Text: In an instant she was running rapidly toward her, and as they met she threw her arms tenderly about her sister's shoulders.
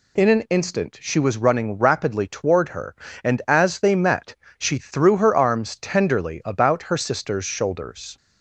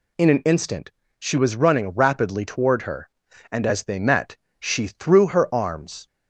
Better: first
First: pauses between "met" and "she"; slight; at 4.3 s; 0.22 s long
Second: pauses between "instant" and "she"; slight; at 0.9 s; 0.26 s long // pauses between "met" and "she"; slight; at 4.3 s; 0.24 s long // stops before "tenderly about her sister's shoulders"; at 6.0 s

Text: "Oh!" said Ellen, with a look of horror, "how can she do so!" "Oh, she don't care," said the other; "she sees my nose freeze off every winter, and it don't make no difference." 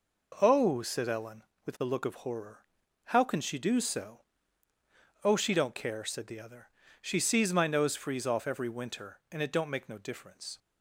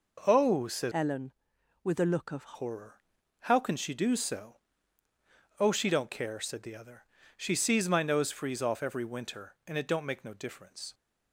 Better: first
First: none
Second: changes voice from "Ellen" to "of"; from 0.9 to 2.5 s; 1.6 s long

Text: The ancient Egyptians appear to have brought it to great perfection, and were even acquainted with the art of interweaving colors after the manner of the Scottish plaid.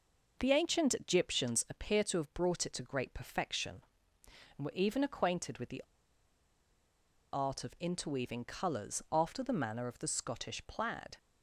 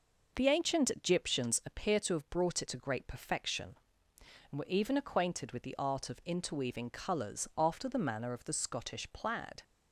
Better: second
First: pauses between "the" and "art"; strong; at 5.8 s; 1.5 s long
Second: none

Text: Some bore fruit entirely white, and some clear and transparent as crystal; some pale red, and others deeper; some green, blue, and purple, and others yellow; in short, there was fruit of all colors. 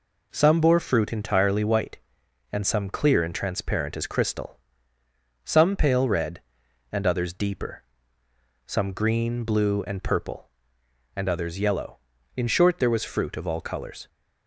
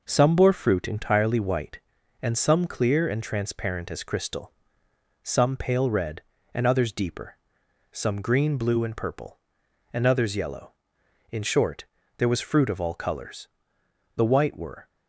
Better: first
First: none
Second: goes on to say "The white were"; noticeable; from 14.1 s on; 0.72 s long

